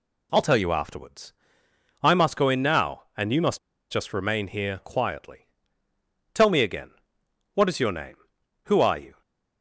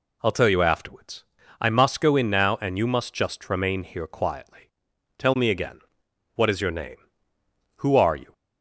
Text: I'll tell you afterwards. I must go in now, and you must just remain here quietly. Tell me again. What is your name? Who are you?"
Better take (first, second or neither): second